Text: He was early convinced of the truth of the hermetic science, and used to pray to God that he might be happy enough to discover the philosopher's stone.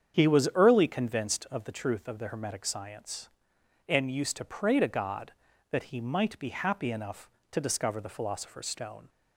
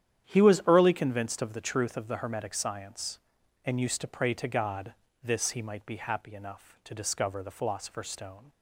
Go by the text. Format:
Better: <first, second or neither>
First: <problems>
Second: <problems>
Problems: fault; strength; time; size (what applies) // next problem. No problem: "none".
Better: first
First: starts louder than the rest; strong; until 1.2 s; 8 dB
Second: starts louder than the rest; strong; until 1.3 s; 10 dB // says "this" for "that"; at 5.2 s